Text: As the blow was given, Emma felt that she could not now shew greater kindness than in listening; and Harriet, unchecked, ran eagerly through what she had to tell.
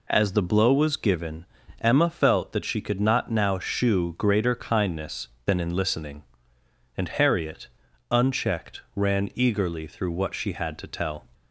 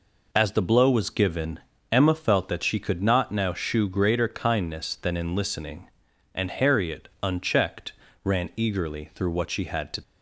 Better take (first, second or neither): first